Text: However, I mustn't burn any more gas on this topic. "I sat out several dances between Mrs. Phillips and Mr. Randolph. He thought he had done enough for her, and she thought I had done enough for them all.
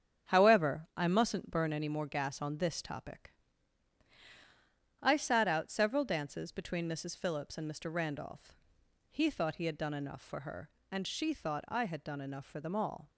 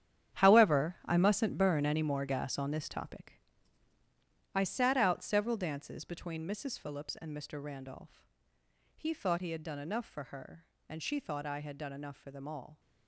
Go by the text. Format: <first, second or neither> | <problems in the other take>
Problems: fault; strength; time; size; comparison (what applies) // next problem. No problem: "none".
first | gets quieter; strong; throughout; 13 dB // starts louder than the rest; strong; until 1.4 s; 9.5 dB; strong in the first